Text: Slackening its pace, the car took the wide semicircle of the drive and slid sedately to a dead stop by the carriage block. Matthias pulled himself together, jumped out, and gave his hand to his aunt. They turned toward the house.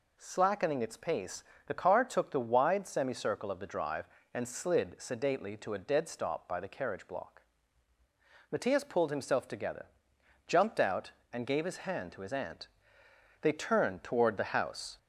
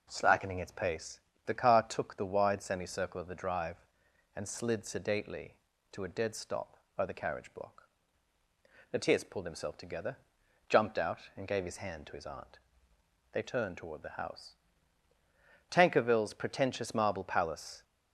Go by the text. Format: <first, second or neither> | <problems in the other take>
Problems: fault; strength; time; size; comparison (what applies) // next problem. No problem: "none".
first | goes on to say "Tankerville's pretentious marble palace"; strong; from 15.6 s on; 2.1 s long